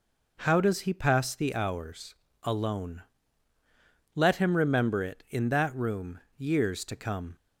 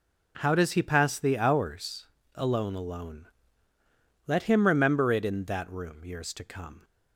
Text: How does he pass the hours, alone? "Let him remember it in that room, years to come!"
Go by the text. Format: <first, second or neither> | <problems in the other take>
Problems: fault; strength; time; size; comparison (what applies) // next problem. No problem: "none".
first | says "alone" twice; at 2.7 s